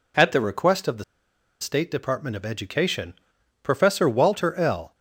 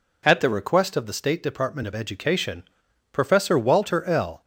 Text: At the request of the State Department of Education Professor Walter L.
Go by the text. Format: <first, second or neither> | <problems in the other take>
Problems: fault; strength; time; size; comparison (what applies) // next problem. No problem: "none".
second | pauses between "the" and "State"; noticeable; at 1.0 s; 0.57 s long // pauses between "Education" and "Professor"; noticeable; at 3.1 s; 0.50 s long; noticeable in the second